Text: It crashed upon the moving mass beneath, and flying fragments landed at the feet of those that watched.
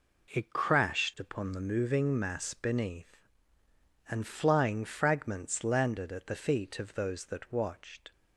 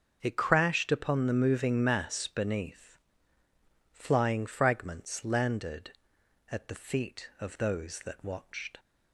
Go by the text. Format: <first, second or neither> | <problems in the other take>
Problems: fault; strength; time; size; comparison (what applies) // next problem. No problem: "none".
first | starts louder than the rest; noticeable; until 1.2 s; 6 dB // skips "and"; at 3.4 s